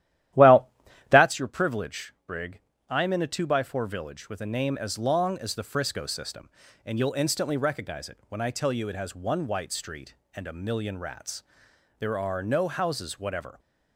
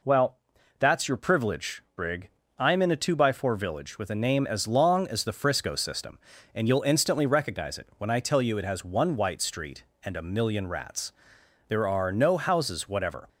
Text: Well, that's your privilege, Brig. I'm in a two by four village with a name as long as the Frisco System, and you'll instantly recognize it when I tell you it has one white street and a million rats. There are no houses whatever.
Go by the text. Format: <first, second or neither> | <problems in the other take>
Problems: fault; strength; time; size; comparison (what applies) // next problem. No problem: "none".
second | starts louder than the rest; strong; until 1.3 s; 12.5 dB